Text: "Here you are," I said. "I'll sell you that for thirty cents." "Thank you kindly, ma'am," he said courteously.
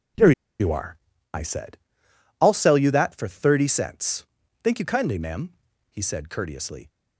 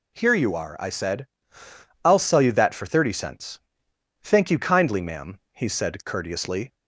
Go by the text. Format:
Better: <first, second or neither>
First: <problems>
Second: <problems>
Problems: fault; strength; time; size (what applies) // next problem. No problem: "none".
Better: second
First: pauses between "Here" and "you"; slight; at 0.3 s; 0.28 s long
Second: none